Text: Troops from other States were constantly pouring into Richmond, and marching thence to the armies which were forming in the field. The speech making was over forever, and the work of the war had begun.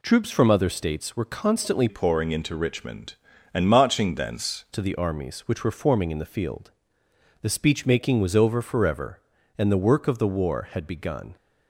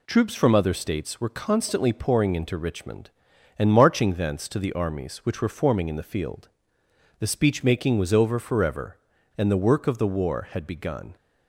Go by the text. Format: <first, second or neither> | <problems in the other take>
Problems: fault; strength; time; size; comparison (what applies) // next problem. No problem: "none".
second | changes voice from "pouring" to "thence"; from 1.8 to 4.6 s; 2.8 s long